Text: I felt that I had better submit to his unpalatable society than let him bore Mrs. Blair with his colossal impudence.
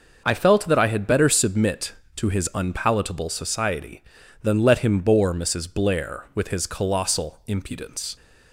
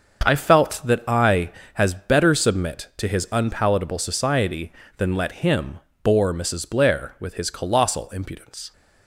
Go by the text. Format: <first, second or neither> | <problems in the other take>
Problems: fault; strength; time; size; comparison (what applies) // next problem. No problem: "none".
first | starts louder than the rest; until 1.3 s; 6.5 dB // says "has" for "had"; at 1.7 s // pauses between "him" and "bore"; slight; at 5.8 s; 0.24 s long